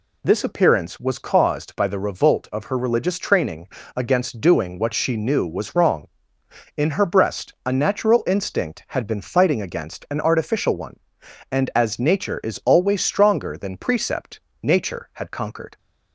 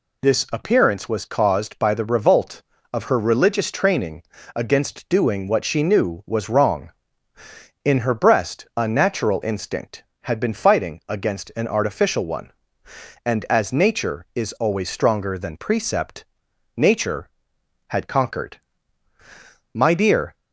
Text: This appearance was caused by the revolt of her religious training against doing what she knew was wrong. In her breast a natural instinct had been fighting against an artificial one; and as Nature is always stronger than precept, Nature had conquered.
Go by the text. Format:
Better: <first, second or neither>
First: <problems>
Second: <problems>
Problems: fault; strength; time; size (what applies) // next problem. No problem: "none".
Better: first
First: pauses between "training" and "against"; slight; at 3.6 s; 0.26 s long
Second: pauses between "training" and "against"; slight; at 4.2 s; 0.32 s long // goes on to say "My dear"; noticeable; from 19.7 s on; 0.62 s long